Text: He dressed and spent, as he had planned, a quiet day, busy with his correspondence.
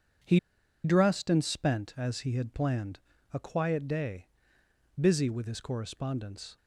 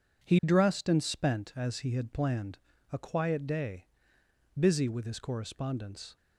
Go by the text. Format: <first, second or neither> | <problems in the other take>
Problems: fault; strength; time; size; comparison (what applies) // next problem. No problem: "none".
second | pauses between "He" and "dressed"; at 0.3 s; 0.44 s long